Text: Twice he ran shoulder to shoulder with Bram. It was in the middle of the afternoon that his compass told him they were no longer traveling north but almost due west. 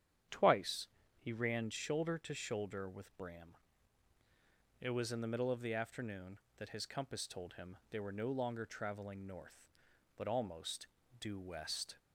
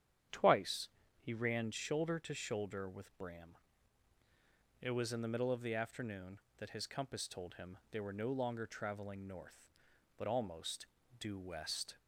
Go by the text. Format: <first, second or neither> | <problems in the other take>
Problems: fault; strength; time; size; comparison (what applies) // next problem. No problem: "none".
neither | starts louder than the rest; strong; the same in both // pauses between "Twice" and "he"; slight; the same in both // pauses between "almost" and "due"; slight; the same in both